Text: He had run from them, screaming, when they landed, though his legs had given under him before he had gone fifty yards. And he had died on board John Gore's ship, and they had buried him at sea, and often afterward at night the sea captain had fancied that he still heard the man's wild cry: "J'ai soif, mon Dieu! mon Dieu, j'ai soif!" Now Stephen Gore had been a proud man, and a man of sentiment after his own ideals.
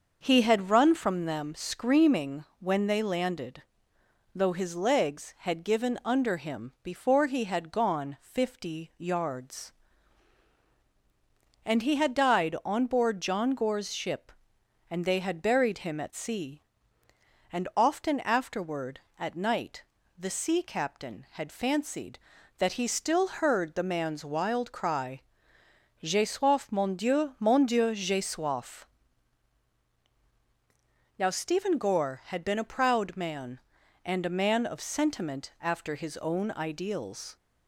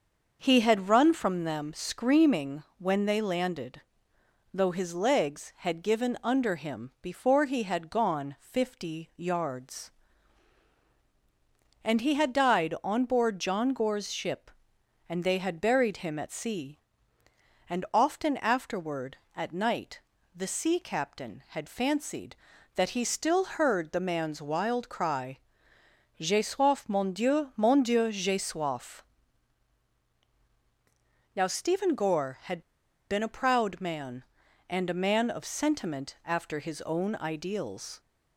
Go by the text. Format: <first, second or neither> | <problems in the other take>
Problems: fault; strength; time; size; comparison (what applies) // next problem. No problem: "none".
first | starts louder than the rest; until 1.4 s; 6 dB; also in the first // pauses between "night" and "the"; slight; at 20.0 s; 0.34 s long; slight in the first // pauses between "had" and "been"; noticeable; at 32.6 s; 0.49 s long